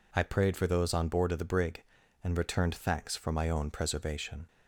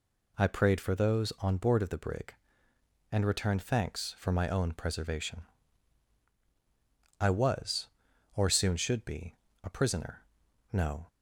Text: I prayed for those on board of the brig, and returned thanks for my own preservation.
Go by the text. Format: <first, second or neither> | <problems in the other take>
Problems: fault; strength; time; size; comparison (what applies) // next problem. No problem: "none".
first | goes on to say "I was or soon should be a prisoner no"; strong; from 7.2 s on; 3.8 s long